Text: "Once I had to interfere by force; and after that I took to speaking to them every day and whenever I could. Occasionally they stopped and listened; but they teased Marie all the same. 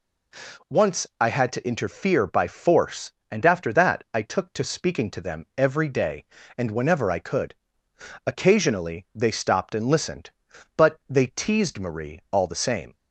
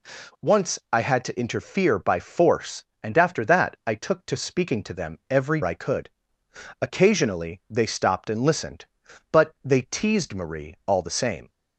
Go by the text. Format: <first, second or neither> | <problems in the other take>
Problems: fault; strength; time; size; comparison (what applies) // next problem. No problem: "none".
first | skips "day and whenever"; at 5.6 s